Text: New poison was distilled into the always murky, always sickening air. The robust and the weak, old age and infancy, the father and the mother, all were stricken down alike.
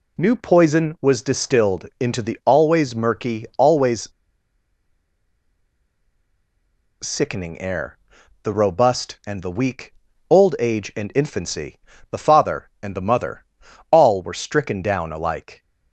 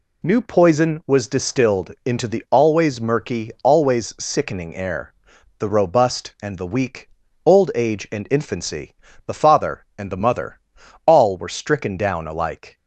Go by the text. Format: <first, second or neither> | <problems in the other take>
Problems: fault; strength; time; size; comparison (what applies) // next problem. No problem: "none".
second | pauses between "always" and "sickening"; strong; at 4.0 s; 2.9 s long